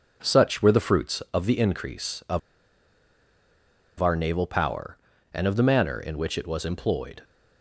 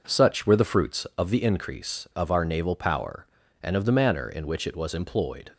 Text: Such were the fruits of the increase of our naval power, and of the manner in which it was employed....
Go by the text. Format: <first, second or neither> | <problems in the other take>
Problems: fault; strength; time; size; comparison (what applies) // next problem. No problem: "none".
second | pauses between "of" and "our"; strong; at 2.3 s; 1.6 s long